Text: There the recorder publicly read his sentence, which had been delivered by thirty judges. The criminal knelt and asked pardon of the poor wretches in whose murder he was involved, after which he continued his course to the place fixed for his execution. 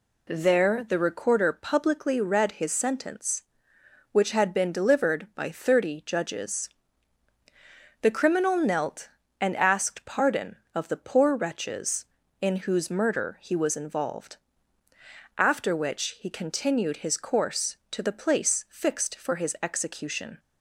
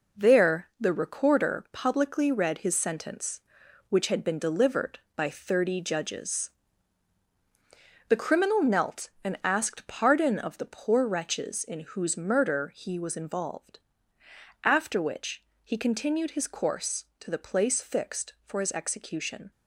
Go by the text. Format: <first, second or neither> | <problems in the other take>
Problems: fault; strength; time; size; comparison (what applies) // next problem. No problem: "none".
first | gets quieter; throughout; 6 dB // pauses between "which" and "he"; slight; at 15.4 s; 0.22 s long